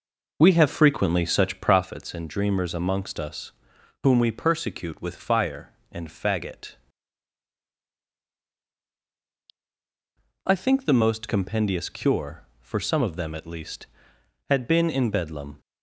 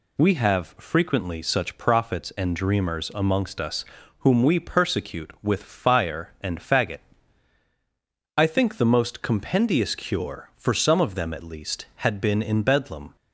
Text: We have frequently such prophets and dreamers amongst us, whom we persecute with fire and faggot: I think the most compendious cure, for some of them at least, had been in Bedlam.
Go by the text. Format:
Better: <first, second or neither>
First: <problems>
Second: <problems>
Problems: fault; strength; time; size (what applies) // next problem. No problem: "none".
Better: second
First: starts louder than the rest; noticeable; until 1.9 s; 5 dB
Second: none